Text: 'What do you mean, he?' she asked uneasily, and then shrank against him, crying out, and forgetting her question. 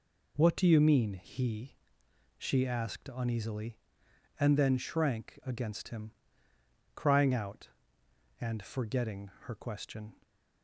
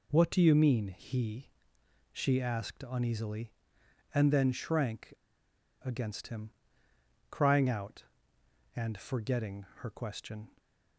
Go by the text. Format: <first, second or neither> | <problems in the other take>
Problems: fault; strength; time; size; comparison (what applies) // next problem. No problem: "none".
first | pauses between "shrank" and "against"; noticeable; at 5.1 s; 0.70 s long